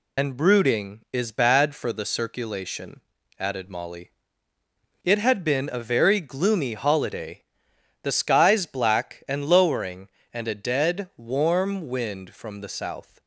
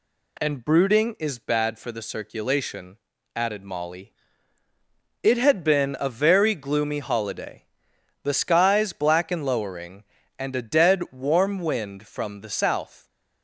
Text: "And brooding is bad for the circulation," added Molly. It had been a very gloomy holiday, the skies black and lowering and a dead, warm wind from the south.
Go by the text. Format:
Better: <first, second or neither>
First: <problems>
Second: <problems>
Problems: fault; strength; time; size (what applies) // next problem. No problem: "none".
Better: second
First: loses the start of "And"; at 0.1 s; 40 ms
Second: none